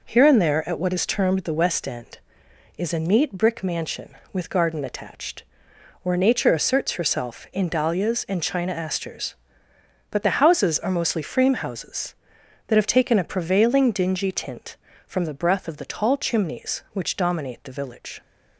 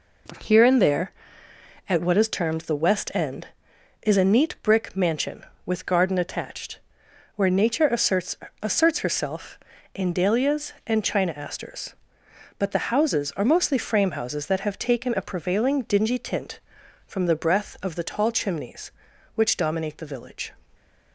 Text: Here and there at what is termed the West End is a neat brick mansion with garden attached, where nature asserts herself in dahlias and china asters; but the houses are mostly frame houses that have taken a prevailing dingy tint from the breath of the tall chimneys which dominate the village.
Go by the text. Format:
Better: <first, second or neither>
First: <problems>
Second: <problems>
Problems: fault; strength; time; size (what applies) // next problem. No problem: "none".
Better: first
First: none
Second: says "asserts" twice; at 8.6 s